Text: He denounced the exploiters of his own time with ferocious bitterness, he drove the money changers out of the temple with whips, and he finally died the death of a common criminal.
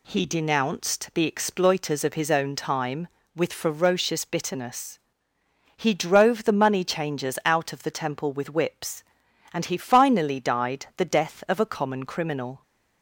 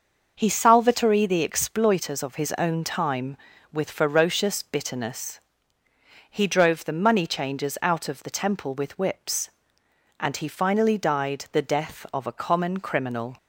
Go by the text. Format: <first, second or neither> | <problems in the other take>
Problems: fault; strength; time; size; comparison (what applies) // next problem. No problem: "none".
first | starts louder than the rest; noticeable; until 1.3 s; 6 dB // says "salvatory" for "denounced"; at 0.4 s